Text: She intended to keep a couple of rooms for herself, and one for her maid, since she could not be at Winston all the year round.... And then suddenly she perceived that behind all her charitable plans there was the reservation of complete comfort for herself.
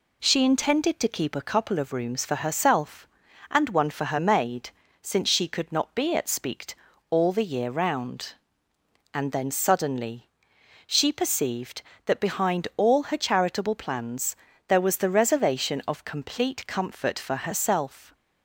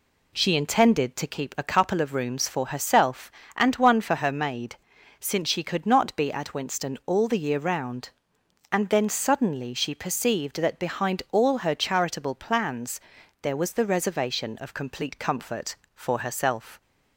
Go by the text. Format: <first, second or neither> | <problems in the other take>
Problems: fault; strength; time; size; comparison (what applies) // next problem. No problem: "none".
second | says "Speakt" for "Winston"; at 6.2 s // pauses between "suddenly" and "she"; noticeable; at 10.2 s; 0.58 s long // pauses between "plans" and "there"; slight; at 14.3 s; 0.32 s long; also in the second